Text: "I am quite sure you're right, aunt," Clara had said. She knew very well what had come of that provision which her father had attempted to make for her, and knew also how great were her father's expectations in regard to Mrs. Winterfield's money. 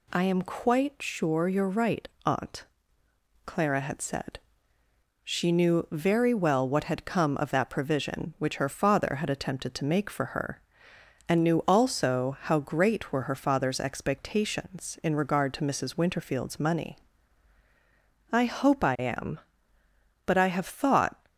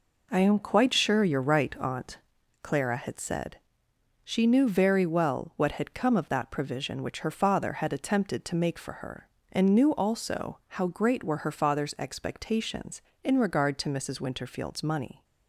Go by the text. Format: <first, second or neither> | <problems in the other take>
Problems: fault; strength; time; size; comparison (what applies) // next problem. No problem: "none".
second | goes on to say "I hope I am but I have thought"; strong; from 18.3 s on; 2.8 s long